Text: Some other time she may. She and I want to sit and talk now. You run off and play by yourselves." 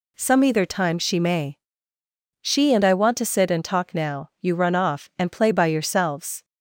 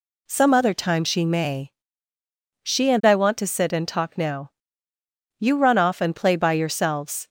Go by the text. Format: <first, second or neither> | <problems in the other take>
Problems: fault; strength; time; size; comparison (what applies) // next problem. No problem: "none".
second | says "either" for "other"; at 0.4 s